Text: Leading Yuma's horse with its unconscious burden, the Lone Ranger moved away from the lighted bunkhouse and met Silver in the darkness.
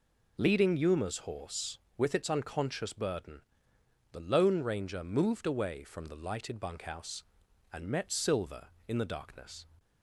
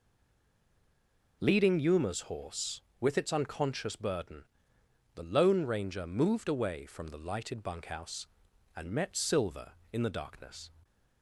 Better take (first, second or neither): first